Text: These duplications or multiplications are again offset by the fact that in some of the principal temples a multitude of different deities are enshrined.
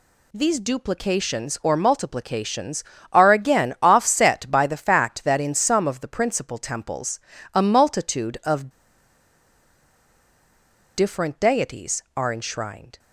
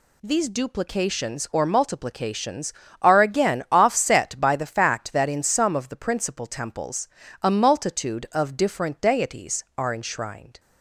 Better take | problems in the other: second | pauses between "temples" and "a"; slight; at 7.1 s; 0.34 s long; slight in the second // pauses between "of" and "different"; strong; at 8.6 s; 2.2 s long

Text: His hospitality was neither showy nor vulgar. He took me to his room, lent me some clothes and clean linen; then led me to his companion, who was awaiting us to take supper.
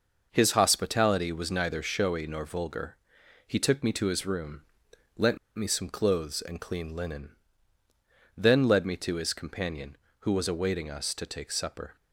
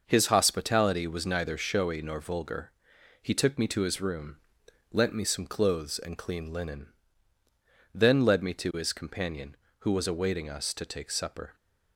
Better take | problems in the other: second | pauses between "lent" and "me"; slight; at 5.3 s; 0.19 s long

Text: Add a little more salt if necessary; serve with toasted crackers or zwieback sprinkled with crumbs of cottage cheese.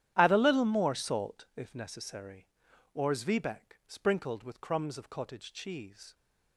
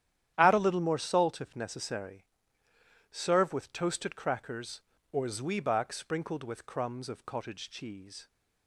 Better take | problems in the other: second | starts louder than the rest; strong; until 1.1 s; 11.5 dB; strong in the second // skips "serve with toasted crackers"; at 2.7 s

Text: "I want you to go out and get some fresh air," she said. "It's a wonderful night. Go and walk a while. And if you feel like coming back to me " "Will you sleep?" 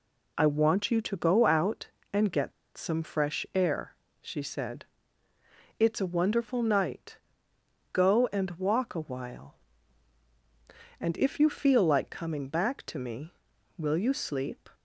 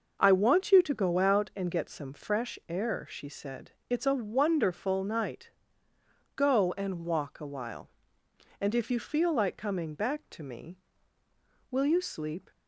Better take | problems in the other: second | pauses between "get" and "some"; slight; at 2.5 s; 0.25 s long

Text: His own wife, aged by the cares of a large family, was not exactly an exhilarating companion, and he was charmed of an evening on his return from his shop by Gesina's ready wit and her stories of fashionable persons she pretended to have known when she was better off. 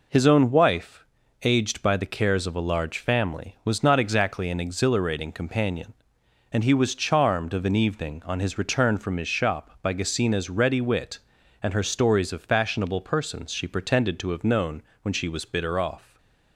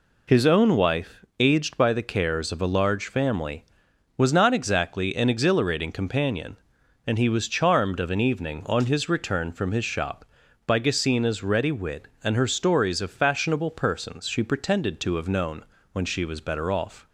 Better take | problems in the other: second | pauses between "known" and "when"; slight; at 14.8 s; 0.22 s long; slight in the second // says "bitter" for "better"; at 15.4 s // stays silent after the last word; slight; from 16.0 s on; 0.5 s long

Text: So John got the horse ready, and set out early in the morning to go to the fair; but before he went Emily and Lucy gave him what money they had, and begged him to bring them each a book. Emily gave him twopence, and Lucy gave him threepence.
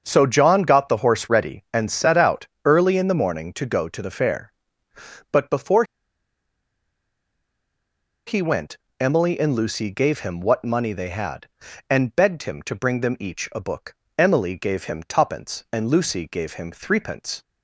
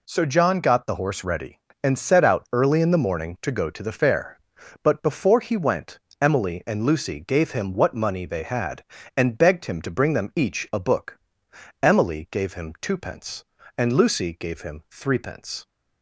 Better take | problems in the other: second | starts louder than the rest; until 1.0 s; 7 dB // pauses between "out" and "early"; slight; at 2.4 s; 0.20 s long // pauses between "before" and "he"; strong; at 5.8 s; 2.4 s long // pauses between "went" and "Emily"; slight; at 8.7 s; 0.22 s long; slight in the second

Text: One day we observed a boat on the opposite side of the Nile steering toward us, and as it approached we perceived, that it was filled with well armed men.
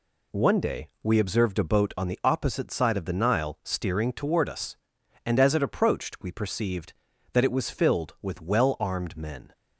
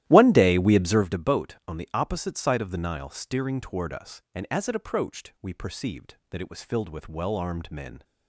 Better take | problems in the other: first | starts louder than the rest; strong; until 1.2 s; 14 dB

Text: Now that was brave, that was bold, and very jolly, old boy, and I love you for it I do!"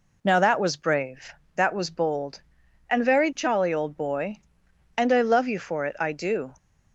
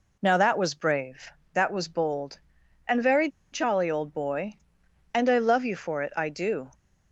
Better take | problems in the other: first | pauses between "very" and "jolly"; slight; at 3.2 s; 0.24 s long

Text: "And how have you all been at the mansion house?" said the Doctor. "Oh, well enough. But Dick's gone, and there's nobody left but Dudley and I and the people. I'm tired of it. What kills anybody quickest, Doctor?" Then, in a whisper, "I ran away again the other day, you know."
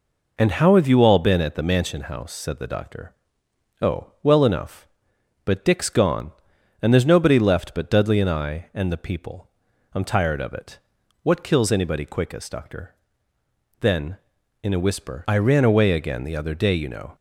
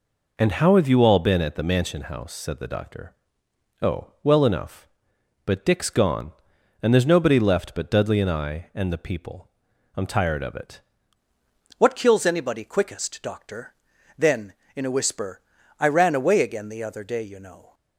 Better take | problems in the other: first | changes voice at "What"; from 11.7 s on; 6.0 s long

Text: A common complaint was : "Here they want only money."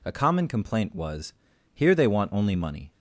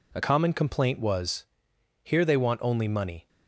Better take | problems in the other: first | changes voice at "common"; from 0.2 s on; 3.0 s long

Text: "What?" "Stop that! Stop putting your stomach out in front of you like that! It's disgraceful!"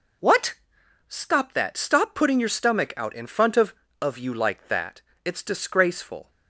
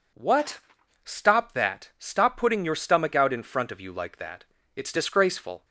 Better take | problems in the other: second | says "of" twice; at 4.0 s

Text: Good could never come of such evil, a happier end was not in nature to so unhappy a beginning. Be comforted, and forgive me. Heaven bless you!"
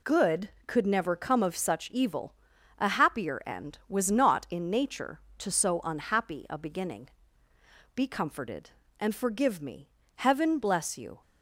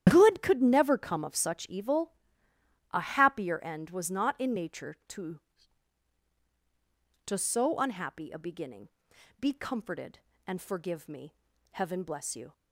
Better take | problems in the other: first | starts louder than the rest; strong; until 1.0 s; 10.5 dB // says "to" twice; at 7.2 s

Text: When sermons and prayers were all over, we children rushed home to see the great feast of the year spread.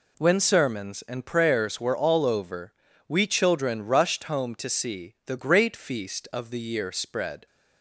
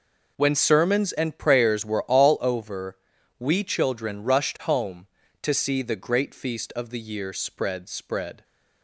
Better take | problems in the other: first | says "spread" twice; at 7.8 s

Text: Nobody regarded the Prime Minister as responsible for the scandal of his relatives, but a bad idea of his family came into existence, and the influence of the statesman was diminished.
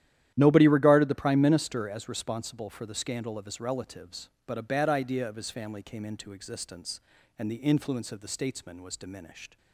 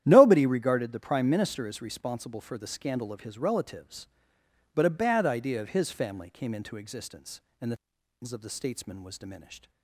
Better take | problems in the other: first | starts louder than the rest; strong; until 1.0 s; 11.5 dB; strong in the first // skips "influence"; at 8.0 s

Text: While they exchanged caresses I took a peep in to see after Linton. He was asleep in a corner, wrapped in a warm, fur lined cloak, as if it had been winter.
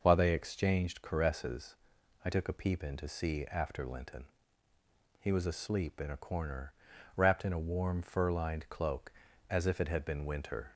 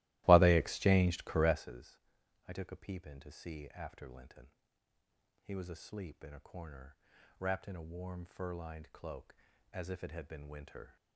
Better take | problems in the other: first | starts louder than the rest; strong; until 1.7 s; 17 dB // pauses between "caresses" and "I"; noticeable; at 1.9 s; 0.50 s long; noticeable in the first

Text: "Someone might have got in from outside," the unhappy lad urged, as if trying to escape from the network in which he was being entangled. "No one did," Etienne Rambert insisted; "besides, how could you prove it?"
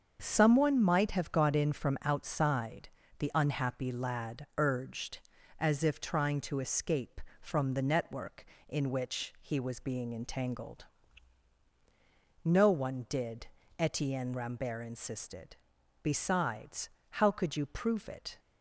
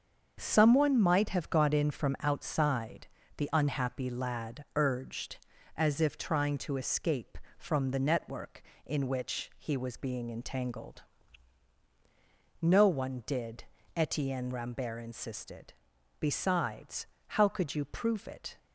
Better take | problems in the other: neither | starts louder than the rest; the same in both

